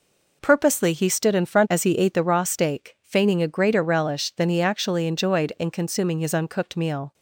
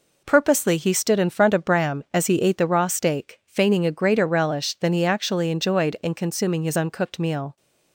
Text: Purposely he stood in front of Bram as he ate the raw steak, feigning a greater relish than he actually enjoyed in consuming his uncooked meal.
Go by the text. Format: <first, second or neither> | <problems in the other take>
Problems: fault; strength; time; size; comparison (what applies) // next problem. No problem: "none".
second | skips "of Bram"; at 1.6 s